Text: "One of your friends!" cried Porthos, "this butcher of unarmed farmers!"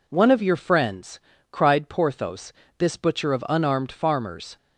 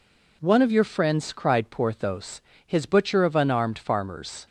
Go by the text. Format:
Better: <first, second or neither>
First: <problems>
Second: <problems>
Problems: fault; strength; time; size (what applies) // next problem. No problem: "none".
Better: first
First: none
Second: says "his" for "this"; at 2.6 s